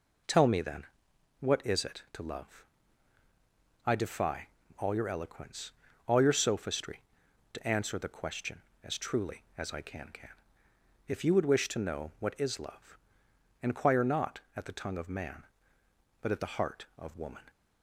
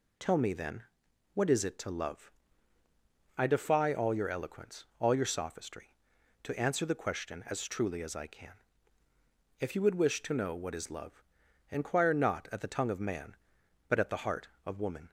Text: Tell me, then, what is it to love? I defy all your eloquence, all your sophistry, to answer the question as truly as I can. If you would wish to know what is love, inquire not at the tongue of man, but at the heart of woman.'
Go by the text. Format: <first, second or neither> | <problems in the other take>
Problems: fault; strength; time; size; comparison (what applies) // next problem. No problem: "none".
second | pauses between "defy" and "all"; slight; at 4.4 s; 0.30 s long // says "can" twice; at 10.1 s